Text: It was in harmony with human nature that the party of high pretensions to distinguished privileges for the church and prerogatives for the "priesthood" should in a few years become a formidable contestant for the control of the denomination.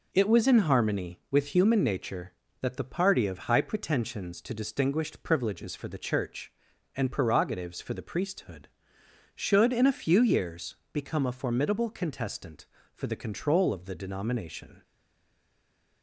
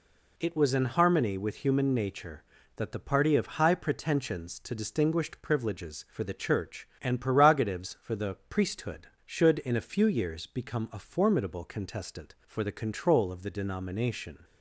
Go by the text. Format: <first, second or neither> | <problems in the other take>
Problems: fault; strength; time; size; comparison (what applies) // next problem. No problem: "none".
second | pauses between "years" and "become"; slight; at 10.7 s; 0.18 s long // stays silent after the last word; noticeable; from 14.8 s on; 1.2 s long